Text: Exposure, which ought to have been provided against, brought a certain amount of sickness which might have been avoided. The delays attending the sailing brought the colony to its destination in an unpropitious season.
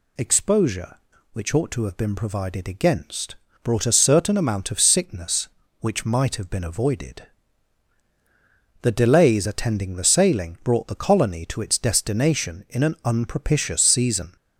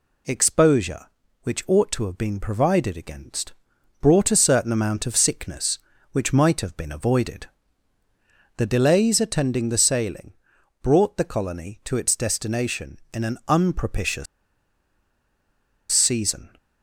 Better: first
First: none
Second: pauses between "sailing" and "brought"; noticeable; at 10.3 s; 0.48 s long // pauses between "unpropitious" and "season"; strong; at 14.2 s; 1.6 s long

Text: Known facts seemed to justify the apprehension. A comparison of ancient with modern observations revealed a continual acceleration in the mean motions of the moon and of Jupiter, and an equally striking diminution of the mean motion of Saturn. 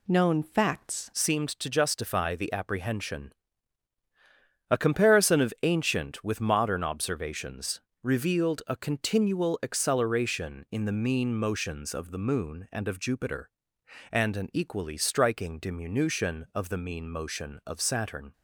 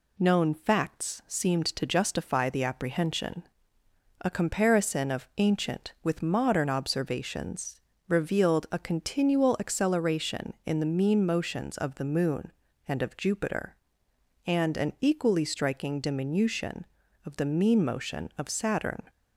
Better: second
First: changes voice at "seemed"; from 1.1 s on; 17.2 s long // pauses between "observations" and "revealed"; slight; at 7.8 s; 0.20 s long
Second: pauses between "observations" and "revealed"; slight; at 7.8 s; 0.28 s long

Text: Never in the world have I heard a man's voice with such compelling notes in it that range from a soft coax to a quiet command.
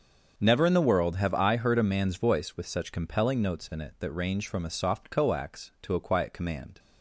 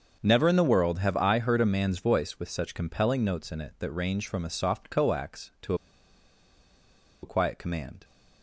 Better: first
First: starts louder than the rest; until 1.3 s; 6.5 dB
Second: starts louder than the rest; until 1.2 s; 6.5 dB // pauses between "to" and "a"; strong; at 5.7 s; 1.4 s long

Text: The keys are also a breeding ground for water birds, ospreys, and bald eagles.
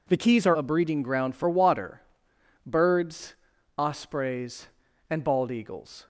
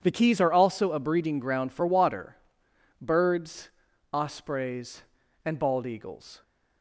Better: second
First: skips "also"; at 0.5 s // pauses between "water" and "birds"; noticeable; at 2.0 s; 0.66 s long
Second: pauses between "water" and "birds"; noticeable; at 2.3 s; 0.66 s long

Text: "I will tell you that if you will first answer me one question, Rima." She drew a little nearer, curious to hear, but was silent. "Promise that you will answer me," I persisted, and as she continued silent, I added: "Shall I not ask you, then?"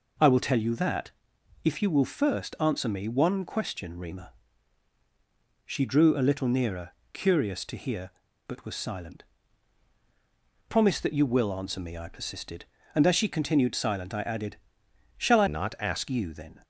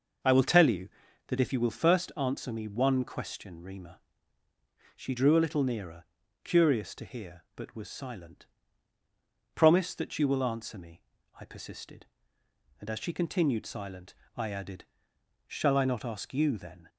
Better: second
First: pauses between "that" and "if"; noticeable; at 1.1 s; 0.52 s long // changes voice from "not" to "ask"; from 15.4 to 16.0 s; 0.6 s long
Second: none

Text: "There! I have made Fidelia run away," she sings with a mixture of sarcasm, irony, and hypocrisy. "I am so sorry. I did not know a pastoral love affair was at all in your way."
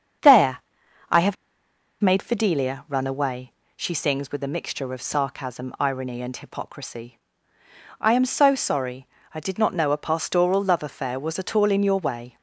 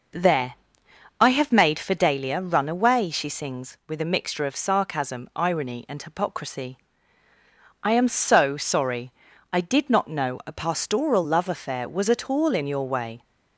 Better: second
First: starts louder than the rest; until 2.3 s; 7 dB // pauses between "have" and "made"; noticeable; at 1.3 s; 0.67 s long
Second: none

